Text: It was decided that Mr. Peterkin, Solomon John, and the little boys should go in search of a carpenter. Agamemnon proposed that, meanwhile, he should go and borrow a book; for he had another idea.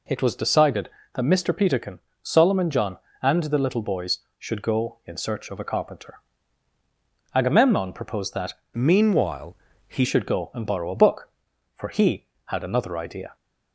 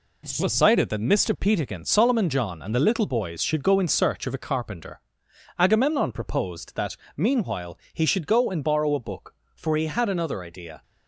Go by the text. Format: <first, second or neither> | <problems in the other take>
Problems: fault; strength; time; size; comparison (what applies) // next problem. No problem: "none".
second | changes voice from "meanwhile" to "he"; from 8.7 to 10.0 s; 1.3 s long